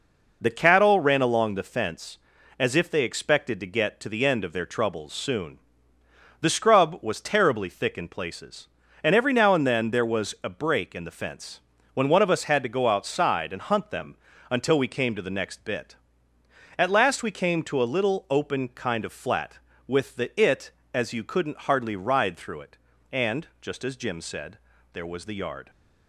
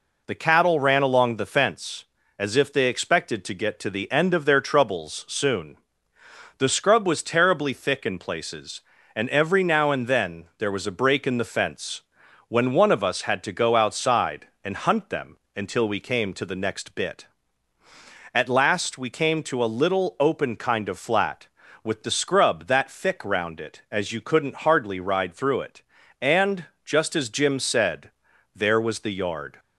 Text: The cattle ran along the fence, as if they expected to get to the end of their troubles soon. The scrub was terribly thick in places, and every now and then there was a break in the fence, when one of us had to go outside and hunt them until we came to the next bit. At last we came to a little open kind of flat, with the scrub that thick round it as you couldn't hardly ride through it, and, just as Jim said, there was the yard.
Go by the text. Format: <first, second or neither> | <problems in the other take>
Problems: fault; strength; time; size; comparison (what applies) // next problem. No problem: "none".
second | pauses between "them" and "until"; slight; at 14.1 s; 0.34 s long; slight in the second // skips "scrub that thick round"; at 20.3 s